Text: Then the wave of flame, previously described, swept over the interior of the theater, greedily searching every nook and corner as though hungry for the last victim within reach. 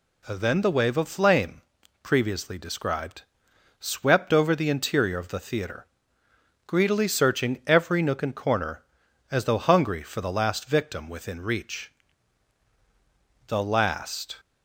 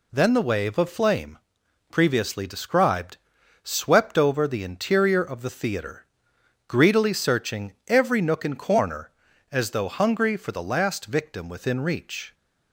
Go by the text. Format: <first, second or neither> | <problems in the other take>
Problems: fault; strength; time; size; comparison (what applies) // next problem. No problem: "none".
second | goes on to say "The last"; noticeable; from 13.4 s on; 0.90 s long